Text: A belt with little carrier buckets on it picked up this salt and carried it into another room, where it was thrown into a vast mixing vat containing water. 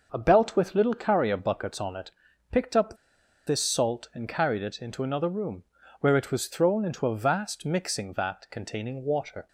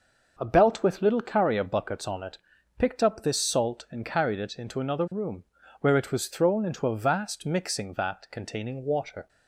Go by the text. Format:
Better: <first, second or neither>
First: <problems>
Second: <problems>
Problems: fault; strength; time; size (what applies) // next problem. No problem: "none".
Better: second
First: starts louder than the rest; noticeable; until 1.1 s; 6 dB // pauses between "it" and "picked"; at 2.0 s; 0.40 s long // pauses between "up" and "this"; noticeable; at 2.9 s; 0.51 s long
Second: starts louder than the rest; noticeable; until 1.3 s; 6 dB // pauses between "it" and "picked"; at 2.3 s; 0.40 s long